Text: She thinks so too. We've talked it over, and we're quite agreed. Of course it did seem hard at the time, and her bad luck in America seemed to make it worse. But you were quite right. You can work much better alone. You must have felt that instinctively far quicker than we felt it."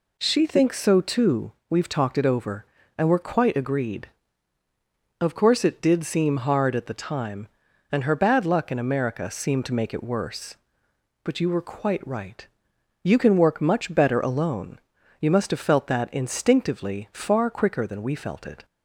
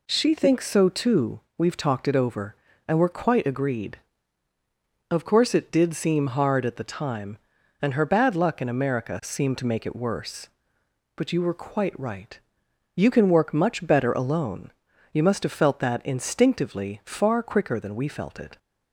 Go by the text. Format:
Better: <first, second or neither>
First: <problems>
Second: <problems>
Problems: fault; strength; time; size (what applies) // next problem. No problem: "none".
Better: neither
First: none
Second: none